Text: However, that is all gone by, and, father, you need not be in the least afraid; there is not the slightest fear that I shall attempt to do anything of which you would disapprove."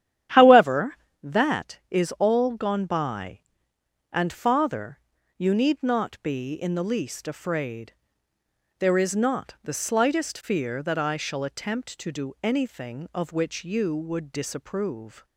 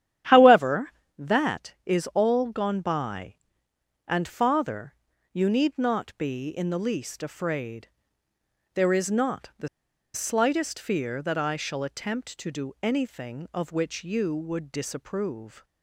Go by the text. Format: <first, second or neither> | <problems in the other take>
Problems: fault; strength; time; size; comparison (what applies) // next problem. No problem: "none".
first | starts louder than the rest; strong; until 1.5 s; 11 dB; strong in the first // pauses between "the" and "slightest"; noticeable; at 9.6 s; 0.46 s long